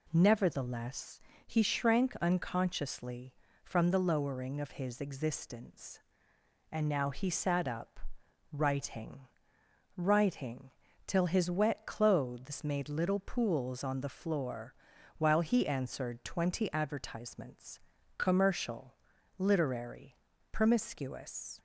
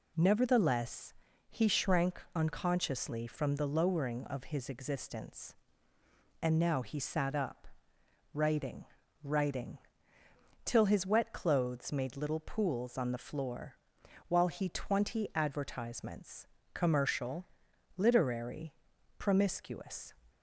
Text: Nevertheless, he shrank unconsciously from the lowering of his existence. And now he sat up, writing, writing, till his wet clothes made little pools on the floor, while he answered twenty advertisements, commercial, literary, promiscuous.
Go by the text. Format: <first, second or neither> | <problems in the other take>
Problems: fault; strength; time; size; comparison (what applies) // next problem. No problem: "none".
first | skips "answered"; at 14.6 s